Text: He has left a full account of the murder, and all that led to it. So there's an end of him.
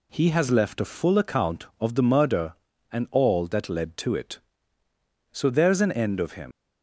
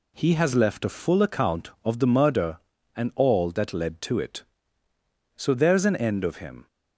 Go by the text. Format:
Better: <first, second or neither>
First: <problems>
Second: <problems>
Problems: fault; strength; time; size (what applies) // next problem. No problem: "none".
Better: second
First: leaves "him" unfinished; at 6.5 s; 115 ms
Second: none